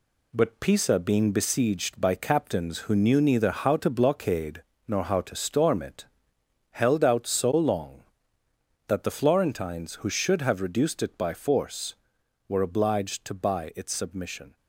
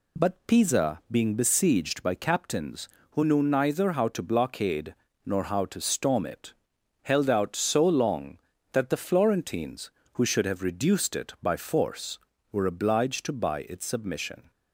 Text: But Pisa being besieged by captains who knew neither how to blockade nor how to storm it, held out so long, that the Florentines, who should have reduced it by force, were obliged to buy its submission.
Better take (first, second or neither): second